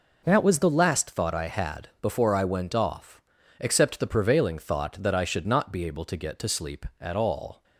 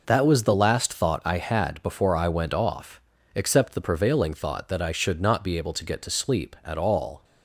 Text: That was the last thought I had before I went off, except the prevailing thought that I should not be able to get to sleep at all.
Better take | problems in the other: neither | none

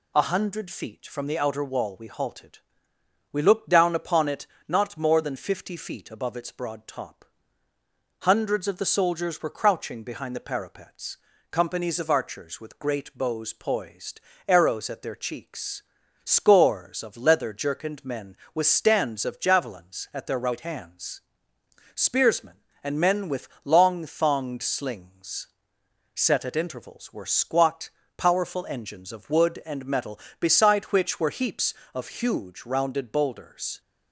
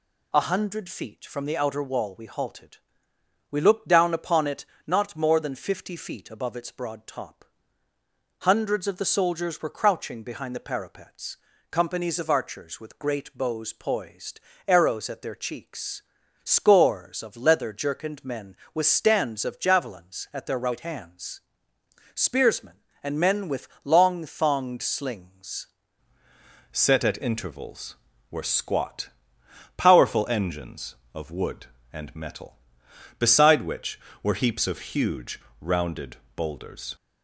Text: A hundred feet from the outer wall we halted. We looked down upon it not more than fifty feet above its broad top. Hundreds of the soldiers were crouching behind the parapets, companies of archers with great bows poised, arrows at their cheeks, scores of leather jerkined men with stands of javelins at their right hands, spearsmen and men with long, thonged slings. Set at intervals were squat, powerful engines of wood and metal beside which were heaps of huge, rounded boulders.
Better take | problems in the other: first | pauses between "it" and "not"; slight; at 4.6 s; 0.20 s long; slight in the first // pauses between "with" and "long"; slight; at 23.6 s; 0.16 s long; slight in the first // changes voice at "Set"; from 26.7 s on; 10.2 s long // pauses between "rounded" and "boulders"; slight; at 36.1 s; 0.20 s long

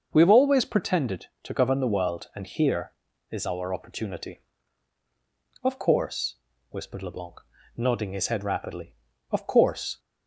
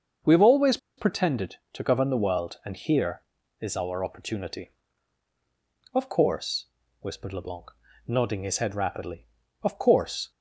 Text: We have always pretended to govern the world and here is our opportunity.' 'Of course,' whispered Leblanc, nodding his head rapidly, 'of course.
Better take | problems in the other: first | starts louder than the rest; until 1.4 s; 6 dB; also in the first // pauses between "always" and "pretended"; slight; at 0.7 s; 0.20 s long

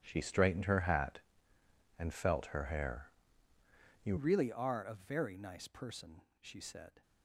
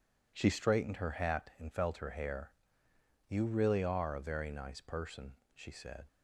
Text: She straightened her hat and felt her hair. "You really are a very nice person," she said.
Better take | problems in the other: second | starts louder than the rest; strong; until 1.0 s; 11 dB // changes voice at "really"; from 4.1 s on; 2.9 s long

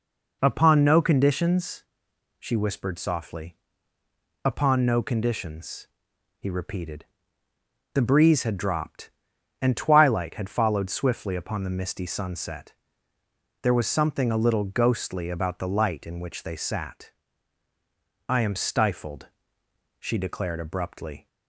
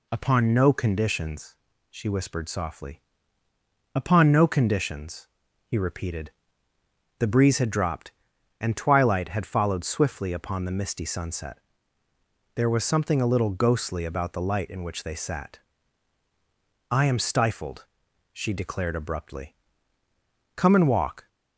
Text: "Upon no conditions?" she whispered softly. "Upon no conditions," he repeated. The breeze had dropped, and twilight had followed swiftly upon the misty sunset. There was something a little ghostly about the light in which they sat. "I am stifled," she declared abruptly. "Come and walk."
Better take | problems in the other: second | stops before "Come and walk"; at 21.2 s

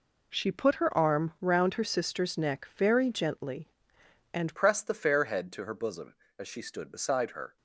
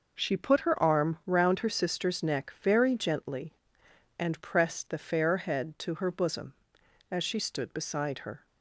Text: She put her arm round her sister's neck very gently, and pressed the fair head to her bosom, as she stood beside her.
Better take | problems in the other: second | changes voice at "pressed"; from 4.5 s on; 3.0 s long

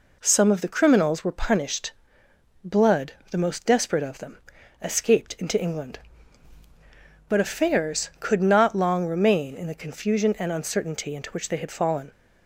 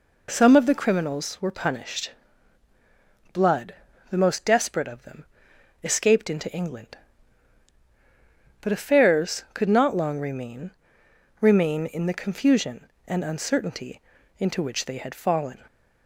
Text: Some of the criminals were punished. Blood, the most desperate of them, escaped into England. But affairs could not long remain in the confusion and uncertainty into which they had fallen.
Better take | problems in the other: first | says "remain" twice; at 11.4 s // pauses between "uncertainty" and "into"; slight; at 14.0 s; 0.36 s long

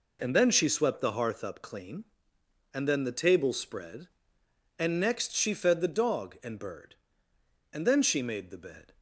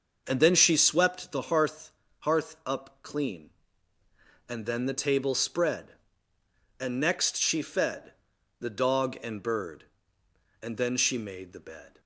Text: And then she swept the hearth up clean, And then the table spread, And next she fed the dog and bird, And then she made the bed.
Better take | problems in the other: first | starts louder than the rest; noticeable; until 1.2 s; 6 dB // says "hearth" twice; at 2.1 s // pauses between "fed" and "the"; noticeable; at 8.1 s; 0.48 s long

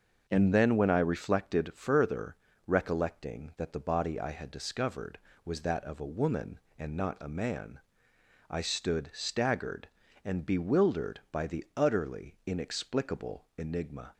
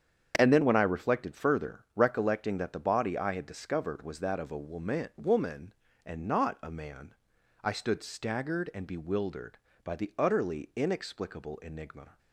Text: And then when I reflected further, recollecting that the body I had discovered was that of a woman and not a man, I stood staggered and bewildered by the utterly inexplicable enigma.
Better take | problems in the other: first | starts louder than the rest; strong; until 1.3 s; 8 dB; noticeable in the first // says "woman" twice; at 5.1 s

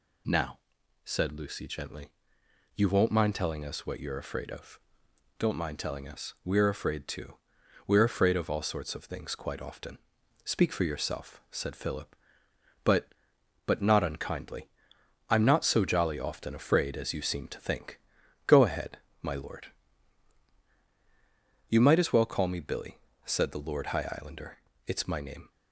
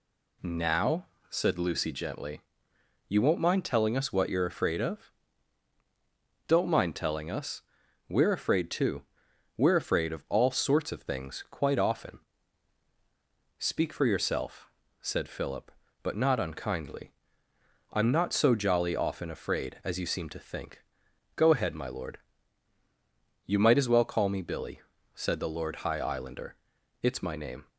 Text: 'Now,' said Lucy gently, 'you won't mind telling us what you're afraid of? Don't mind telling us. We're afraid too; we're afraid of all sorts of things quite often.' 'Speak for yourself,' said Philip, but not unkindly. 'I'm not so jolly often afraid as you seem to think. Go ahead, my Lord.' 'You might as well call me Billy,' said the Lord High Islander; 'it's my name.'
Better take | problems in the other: second | says "but" twice; at 13.6 s

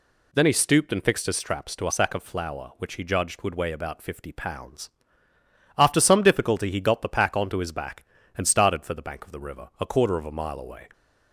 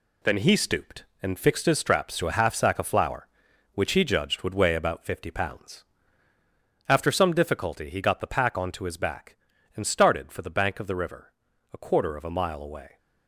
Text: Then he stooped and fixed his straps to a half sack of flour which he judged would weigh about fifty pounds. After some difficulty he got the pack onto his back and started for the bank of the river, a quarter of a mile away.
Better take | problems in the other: second | skips "half"; at 1.9 s

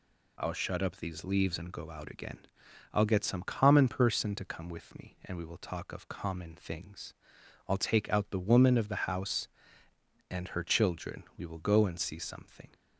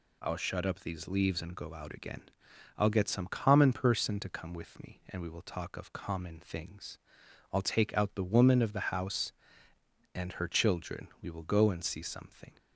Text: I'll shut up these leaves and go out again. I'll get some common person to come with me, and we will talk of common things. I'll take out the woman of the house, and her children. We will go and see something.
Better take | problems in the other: neither | none

